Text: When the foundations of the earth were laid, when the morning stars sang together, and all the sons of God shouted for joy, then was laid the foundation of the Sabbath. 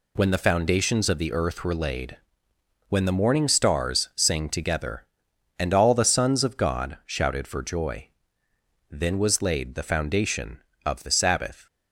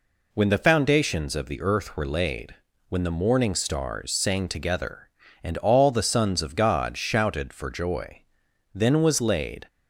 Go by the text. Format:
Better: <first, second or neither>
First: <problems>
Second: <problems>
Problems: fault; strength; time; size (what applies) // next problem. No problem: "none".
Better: first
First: none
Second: stops before "the foundation of the Sabbath"; at 9.6 s